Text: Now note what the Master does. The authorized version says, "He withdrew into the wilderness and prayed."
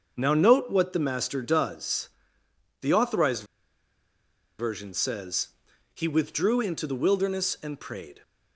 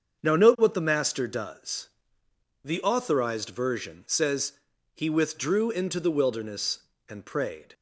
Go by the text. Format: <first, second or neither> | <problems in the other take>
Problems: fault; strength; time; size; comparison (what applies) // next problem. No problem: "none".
second | starts louder than the rest; until 1.1 s; 6.5 dB; also in the second // pauses between "authorized" and "version"; at 3.4 s; 1.1 s long